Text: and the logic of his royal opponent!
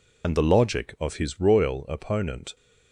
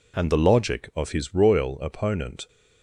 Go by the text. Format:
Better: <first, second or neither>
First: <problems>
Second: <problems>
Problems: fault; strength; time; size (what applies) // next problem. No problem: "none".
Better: second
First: loses the start of "and"; at 0.2 s; 60 ms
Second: none